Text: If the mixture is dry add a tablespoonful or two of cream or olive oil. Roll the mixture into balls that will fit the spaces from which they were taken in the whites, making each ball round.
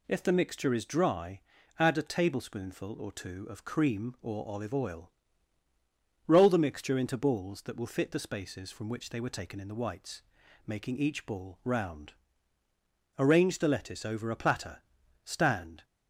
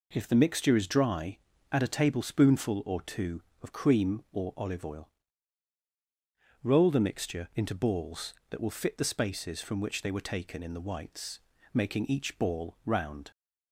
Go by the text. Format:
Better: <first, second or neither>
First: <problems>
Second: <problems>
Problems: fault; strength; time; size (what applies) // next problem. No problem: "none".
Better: second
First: pauses between "dry" and "add"; at 1.4 s; 0.38 s long // goes on to say "Arrange the lettuce over a platter stand"; strong; from 13.1 s on; 2.6 s long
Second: pauses between "dry" and "add"; slight; at 1.3 s; 0.34 s long